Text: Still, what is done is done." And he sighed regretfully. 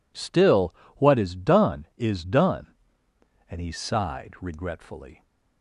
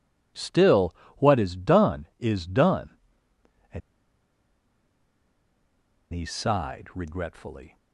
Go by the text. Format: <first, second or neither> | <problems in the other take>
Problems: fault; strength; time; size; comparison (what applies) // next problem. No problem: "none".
first | pauses between "And" and "he"; strong; at 3.8 s; 2.3 s long